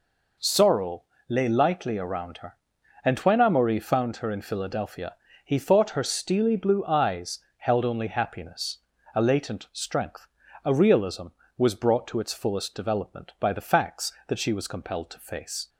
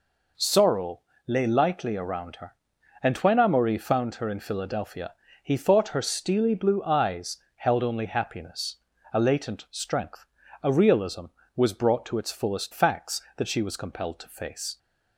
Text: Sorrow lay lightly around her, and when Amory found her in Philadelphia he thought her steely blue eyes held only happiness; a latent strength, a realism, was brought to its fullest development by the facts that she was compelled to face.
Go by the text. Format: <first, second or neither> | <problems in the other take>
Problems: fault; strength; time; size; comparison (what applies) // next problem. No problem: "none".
first | pauses between "Sorrow" and "lay"; slight; at 0.9 s; 0.28 s long; slight in the first // pauses between "Philadelphia" and "he"; slight; at 5.1 s; 0.32 s long; slight in the first // pauses between "eyes" and "held"; slight; at 7.3 s; 0.18 s long; slight in the first // skips "development by the"; at 12.7 s